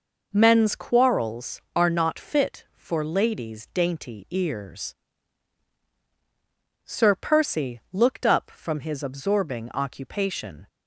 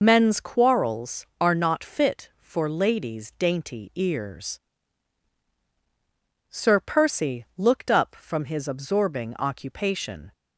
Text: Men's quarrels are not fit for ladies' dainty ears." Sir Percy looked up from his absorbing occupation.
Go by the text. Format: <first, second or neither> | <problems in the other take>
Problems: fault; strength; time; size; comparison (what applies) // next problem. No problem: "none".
first | loses the start of "Men's"; at 0.0 s; 30 ms